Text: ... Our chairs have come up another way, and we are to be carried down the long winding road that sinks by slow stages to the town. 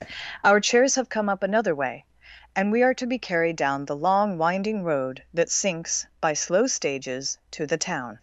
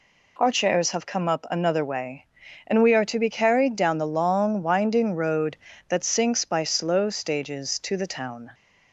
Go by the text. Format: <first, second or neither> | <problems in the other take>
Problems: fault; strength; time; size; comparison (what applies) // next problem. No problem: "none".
second | starts louder than the rest; noticeable; until 1.2 s; 5 dB